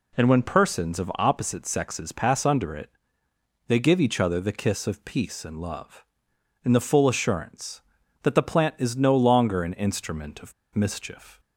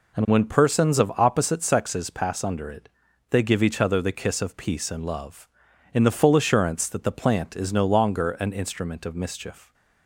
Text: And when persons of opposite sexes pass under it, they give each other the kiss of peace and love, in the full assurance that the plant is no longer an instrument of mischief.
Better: second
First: pauses between "of" and "mischief"; slight; at 10.5 s; 0.22 s long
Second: none

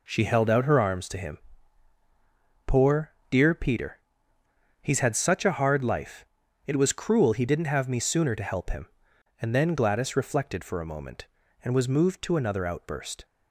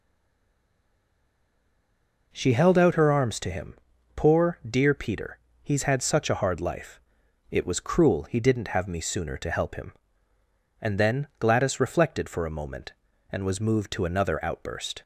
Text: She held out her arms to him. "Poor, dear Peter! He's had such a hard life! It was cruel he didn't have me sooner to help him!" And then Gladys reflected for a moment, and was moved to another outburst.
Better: first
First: none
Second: stays silent before the first word; until 2.3 s; 2.3 s long

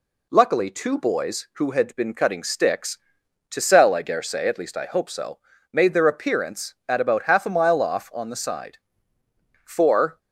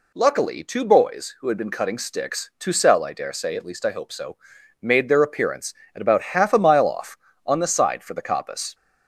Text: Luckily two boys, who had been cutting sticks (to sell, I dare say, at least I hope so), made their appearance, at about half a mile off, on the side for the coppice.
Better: second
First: stops before "the coppice"; at 10.1 s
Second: none

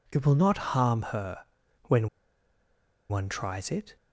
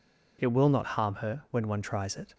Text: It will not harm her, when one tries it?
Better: second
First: pauses between "when" and "one"; at 2.0 s; 1.0 s long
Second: none

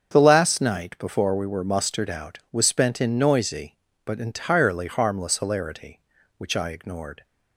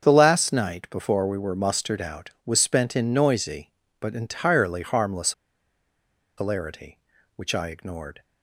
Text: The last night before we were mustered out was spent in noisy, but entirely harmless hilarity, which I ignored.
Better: first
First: starts louder than the rest; strong; until 1.1 s; 7 dB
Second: starts louder than the rest; until 1.0 s; 7 dB // pauses between "harmless" and "hilarity"; at 5.3 s; 1.0 s long

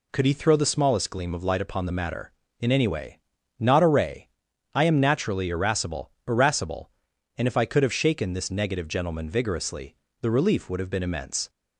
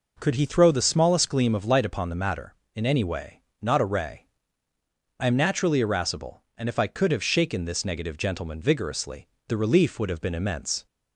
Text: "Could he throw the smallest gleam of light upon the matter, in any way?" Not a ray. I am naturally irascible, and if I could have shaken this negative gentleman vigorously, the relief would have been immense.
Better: second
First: says "irascible" twice; at 6.2 s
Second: none

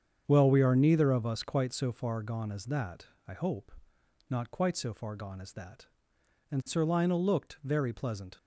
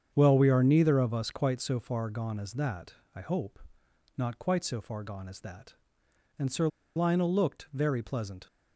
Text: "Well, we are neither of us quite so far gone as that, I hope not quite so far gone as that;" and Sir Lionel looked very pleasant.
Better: first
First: starts louder than the rest; strong; until 1.2 s; 7.5 dB // pauses between "hope" and "not"; noticeable; at 3.7 s; 0.56 s long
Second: starts louder than the rest; strong; until 1.1 s; 7.5 dB // pauses between "hope" and "not"; noticeable; at 3.5 s; 0.56 s long // pauses between "Sir" and "Lionel"; slight; at 6.6 s; 0.27 s long

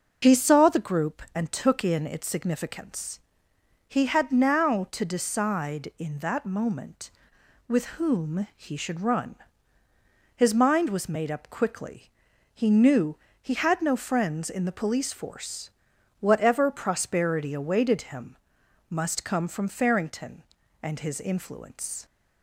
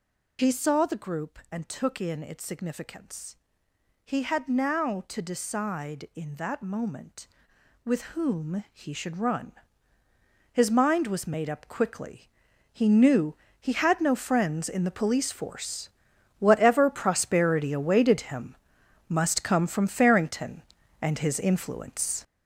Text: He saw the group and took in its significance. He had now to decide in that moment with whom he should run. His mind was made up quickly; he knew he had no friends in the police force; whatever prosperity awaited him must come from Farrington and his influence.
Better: first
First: pauses between "knew" and "he"; slight; at 13.1 s; 0.26 s long // pauses between "him" and "must"; noticeable; at 18.3 s; 0.56 s long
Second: gets louder; strong; throughout; 8 dB // pauses between "knew" and "he"; slight; at 13.3 s; 0.26 s long // pauses between "him" and "must"; noticeable; at 18.5 s; 0.56 s long

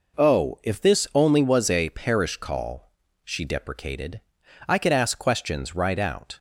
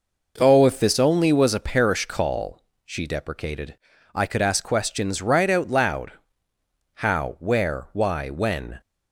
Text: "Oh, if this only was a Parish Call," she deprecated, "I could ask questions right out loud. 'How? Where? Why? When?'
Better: second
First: stops before "loud How Where Why When"; at 6.3 s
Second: none

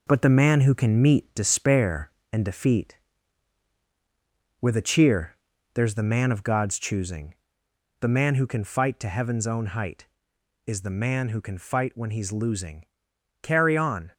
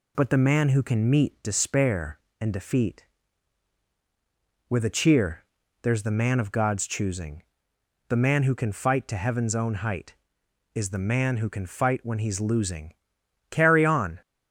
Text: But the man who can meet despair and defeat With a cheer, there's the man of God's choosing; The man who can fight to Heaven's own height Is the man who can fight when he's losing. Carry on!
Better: second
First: gets quieter; noticeable; throughout; 5 dB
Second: none

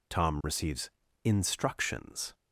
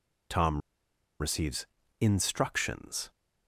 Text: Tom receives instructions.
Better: first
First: pauses between "receives" and "instructions"; slight; at 0.8 s; 0.34 s long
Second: pauses between "Tom" and "receives"; noticeable; at 0.6 s; 0.59 s long // pauses between "receives" and "instructions"; slight; at 1.6 s; 0.34 s long

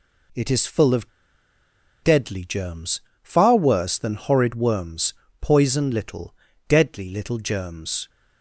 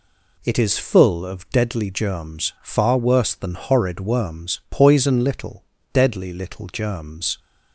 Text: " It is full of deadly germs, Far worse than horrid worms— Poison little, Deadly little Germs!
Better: second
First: pauses between "of" and "deadly"; noticeable; at 1.0 s; 0.93 s long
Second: none

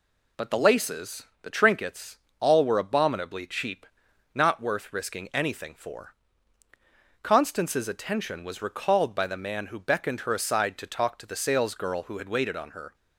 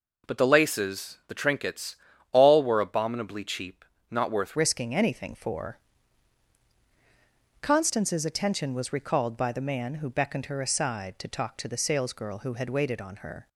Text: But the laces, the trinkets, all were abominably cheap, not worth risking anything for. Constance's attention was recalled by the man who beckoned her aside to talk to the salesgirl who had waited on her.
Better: first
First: none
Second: changes voice at "risking"; from 4.5 s on; 8.9 s long

